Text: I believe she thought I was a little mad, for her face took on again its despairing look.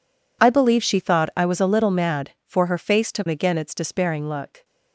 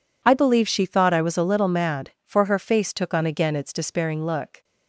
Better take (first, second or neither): second